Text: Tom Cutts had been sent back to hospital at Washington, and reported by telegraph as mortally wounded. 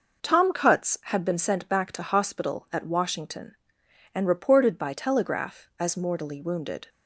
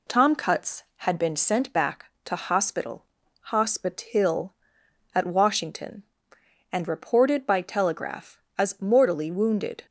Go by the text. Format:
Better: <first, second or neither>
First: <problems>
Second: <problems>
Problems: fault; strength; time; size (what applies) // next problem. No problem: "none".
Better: first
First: none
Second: says "hospital" twice; at 3.4 s